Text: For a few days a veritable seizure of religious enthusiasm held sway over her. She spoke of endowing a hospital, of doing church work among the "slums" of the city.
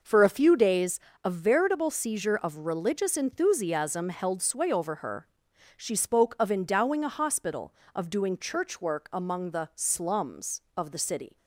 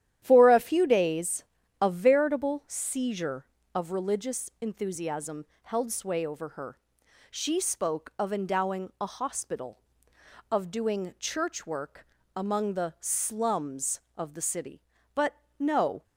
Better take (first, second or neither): first